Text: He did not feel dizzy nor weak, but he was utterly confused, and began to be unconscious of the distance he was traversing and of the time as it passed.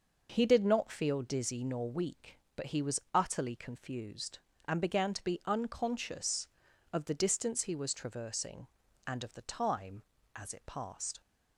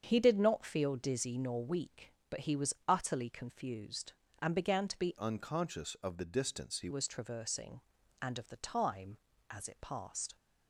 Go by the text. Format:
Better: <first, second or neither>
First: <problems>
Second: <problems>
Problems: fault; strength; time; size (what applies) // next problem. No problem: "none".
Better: first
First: none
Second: starts louder than the rest; strong; until 1.0 s; 7.5 dB // changes voice from "unconscious" to "he"; from 5.1 to 6.8 s; 1.7 s long